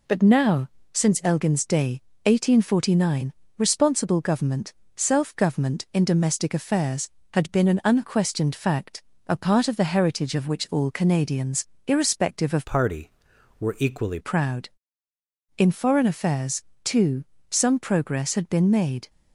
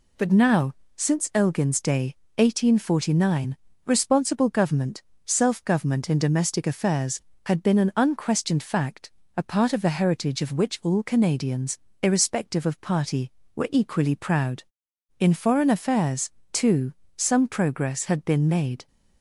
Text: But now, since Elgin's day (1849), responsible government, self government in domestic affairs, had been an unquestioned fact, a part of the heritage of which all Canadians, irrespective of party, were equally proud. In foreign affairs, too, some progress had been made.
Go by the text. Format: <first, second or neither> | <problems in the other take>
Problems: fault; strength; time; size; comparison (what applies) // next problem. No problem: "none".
second | changes voice from "party" to "equally"; from 12.6 to 14.1 s; 1.5 s long